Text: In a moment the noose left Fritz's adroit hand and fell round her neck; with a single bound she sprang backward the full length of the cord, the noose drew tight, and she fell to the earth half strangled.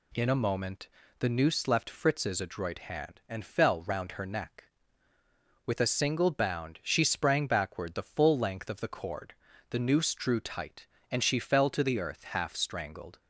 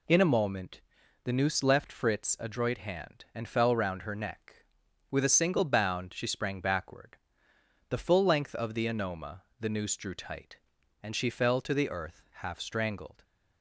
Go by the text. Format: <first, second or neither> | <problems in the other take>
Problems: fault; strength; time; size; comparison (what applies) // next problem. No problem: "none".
first | pauses between "moment" and "the"; at 0.8 s; 0.42 s long; slight in the first // pauses between "backward" and "the"; noticeable; at 7.1 s; 0.72 s long // says "anoma" for "cord"; at 8.8 s